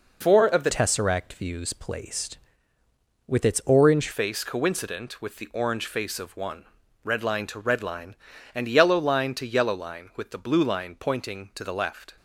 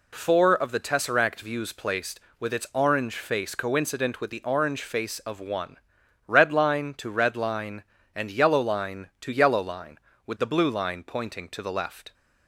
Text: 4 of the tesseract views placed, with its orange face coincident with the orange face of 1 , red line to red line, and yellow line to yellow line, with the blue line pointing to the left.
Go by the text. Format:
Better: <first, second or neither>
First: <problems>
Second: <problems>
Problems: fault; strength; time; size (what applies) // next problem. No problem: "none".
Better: second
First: changes voice from "tesseract" to "orange"; from 0.7 to 4.0 s; 3.3 s long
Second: none